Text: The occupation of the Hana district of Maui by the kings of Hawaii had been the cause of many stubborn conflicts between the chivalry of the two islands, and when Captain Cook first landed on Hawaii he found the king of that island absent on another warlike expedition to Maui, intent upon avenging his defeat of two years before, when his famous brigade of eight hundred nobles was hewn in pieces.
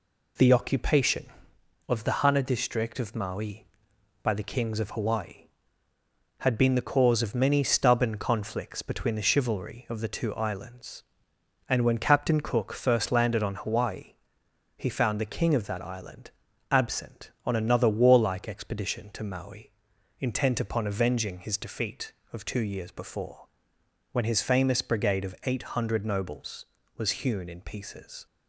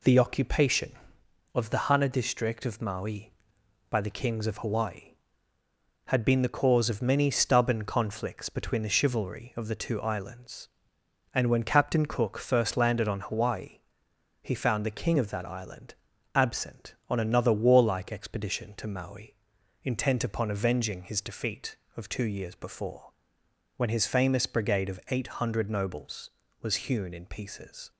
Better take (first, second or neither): neither